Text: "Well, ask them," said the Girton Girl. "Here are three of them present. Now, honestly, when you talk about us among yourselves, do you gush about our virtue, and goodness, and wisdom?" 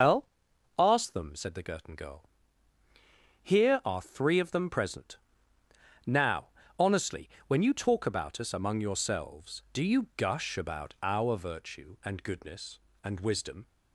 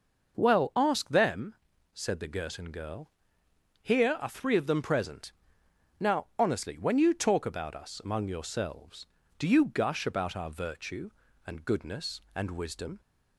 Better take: second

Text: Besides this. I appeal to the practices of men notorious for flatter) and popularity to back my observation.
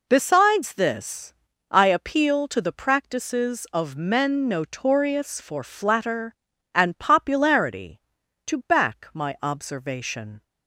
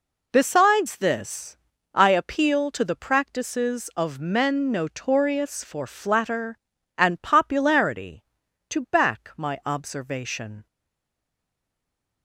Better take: first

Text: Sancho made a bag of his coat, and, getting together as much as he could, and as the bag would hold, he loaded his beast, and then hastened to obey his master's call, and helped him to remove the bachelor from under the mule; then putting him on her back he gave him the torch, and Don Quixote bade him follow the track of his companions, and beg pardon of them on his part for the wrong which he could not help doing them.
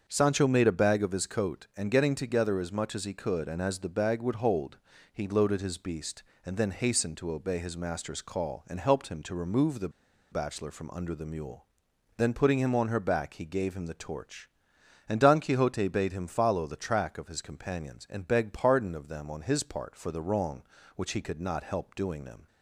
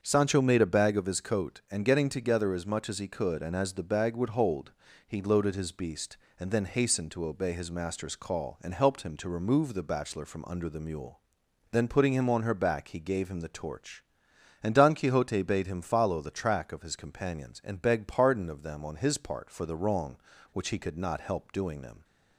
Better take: second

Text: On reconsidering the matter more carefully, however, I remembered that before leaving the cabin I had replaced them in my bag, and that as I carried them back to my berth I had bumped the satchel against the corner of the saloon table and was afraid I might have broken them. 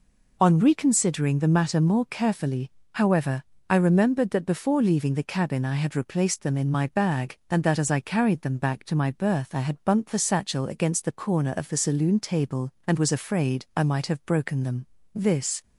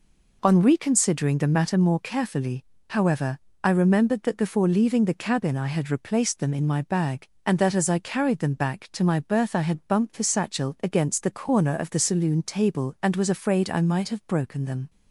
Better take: second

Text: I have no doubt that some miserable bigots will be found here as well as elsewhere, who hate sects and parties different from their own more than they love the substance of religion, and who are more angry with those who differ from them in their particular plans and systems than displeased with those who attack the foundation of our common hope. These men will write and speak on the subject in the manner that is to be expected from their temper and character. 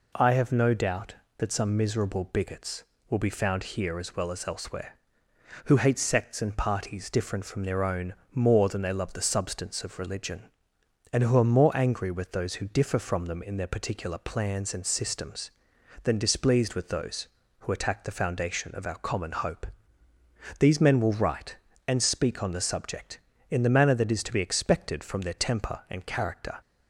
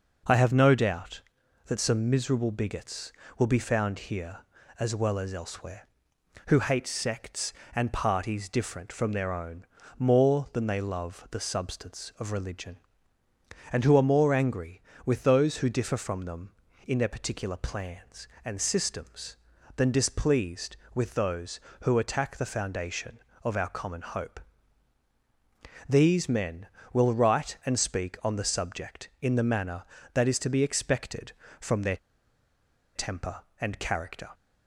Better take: first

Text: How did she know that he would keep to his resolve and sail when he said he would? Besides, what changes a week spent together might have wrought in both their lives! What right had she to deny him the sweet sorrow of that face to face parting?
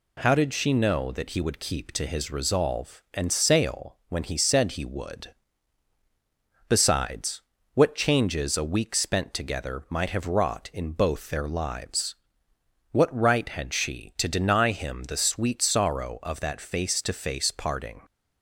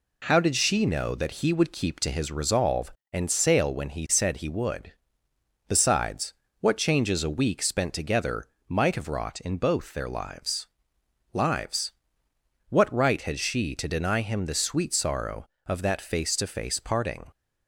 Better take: first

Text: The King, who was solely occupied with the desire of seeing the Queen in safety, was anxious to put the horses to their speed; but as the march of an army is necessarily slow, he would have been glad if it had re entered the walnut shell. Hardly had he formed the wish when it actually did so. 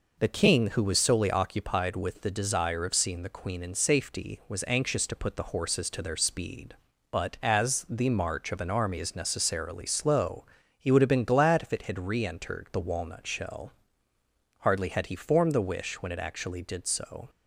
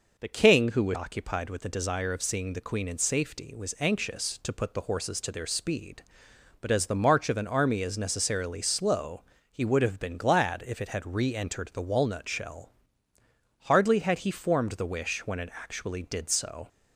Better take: first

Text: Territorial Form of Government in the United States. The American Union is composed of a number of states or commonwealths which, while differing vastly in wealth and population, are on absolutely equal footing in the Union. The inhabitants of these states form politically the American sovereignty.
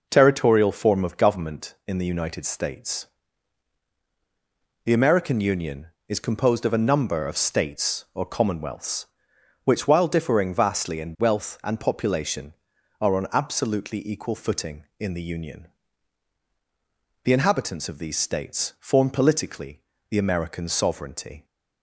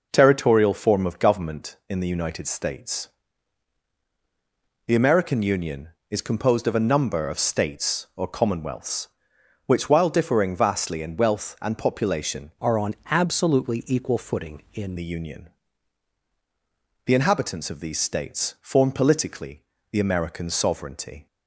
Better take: first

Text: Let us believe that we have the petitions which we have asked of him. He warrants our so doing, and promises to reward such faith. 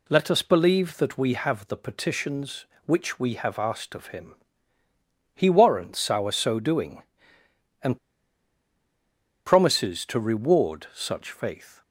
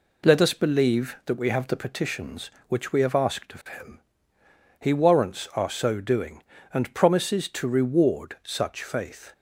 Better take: second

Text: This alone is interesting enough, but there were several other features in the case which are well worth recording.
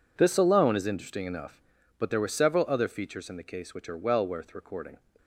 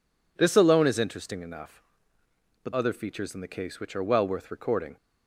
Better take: first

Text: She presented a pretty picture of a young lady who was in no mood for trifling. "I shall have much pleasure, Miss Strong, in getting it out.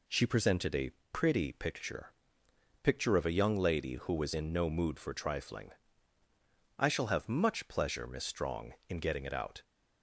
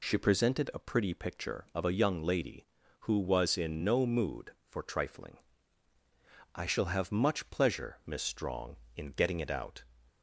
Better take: second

